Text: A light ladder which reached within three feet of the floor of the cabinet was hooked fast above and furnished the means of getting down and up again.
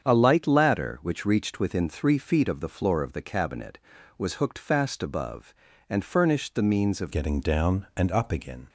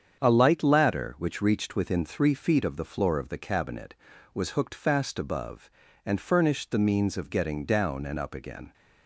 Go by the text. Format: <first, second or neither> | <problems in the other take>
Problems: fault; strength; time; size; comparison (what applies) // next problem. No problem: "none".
second | starts louder than the rest; strong; until 1.1 s; 7.5 dB; strong in the second // changes voice at "getting"; from 7.1 s on; 1.5 s long